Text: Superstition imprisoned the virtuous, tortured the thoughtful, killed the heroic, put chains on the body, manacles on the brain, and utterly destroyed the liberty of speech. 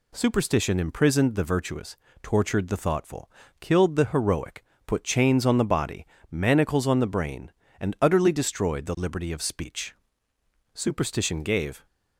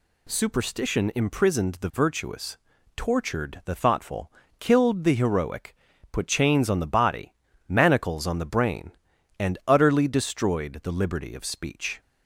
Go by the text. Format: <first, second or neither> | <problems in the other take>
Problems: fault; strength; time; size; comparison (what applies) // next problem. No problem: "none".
second | goes on to say "Superstition gave"; noticeable; from 10.7 s on; 1.1 s long